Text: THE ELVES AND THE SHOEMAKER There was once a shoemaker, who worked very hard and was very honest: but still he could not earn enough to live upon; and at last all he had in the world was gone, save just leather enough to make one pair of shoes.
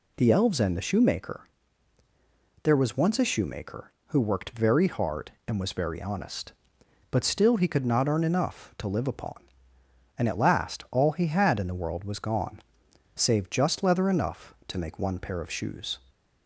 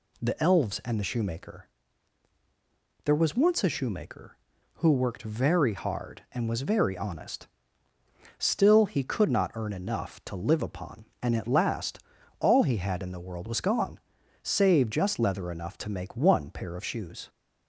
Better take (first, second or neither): first